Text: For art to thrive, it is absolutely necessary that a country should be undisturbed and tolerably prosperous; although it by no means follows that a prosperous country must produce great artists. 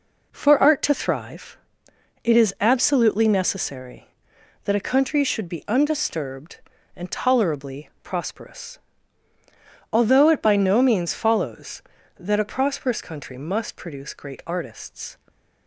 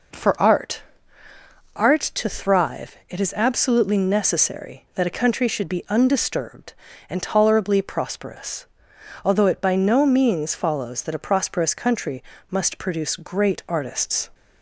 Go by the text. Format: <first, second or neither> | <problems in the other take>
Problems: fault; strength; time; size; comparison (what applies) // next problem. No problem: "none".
first | says "art" twice; at 1.7 s // pauses between "country" and "must"; slight; at 12.2 s; 0.28 s long